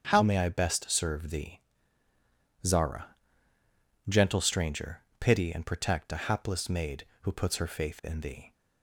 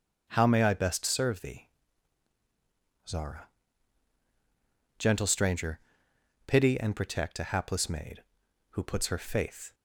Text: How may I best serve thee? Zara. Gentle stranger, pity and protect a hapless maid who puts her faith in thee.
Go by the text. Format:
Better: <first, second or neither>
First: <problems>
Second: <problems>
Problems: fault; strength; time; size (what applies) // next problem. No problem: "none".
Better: first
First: starts louder than the rest; until 1.1 s; 7 dB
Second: starts louder than the rest; strong; until 1.3 s; 7.5 dB // stops before "in thee"; at 9.7 s